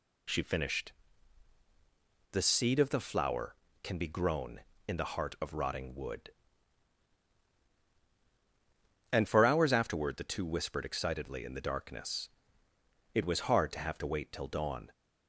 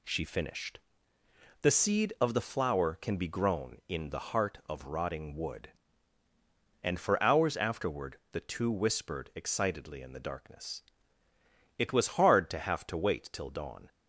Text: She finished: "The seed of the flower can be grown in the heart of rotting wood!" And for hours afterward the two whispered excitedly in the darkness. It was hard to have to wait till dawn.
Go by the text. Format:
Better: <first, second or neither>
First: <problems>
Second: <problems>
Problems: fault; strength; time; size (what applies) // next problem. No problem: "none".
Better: neither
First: none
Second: none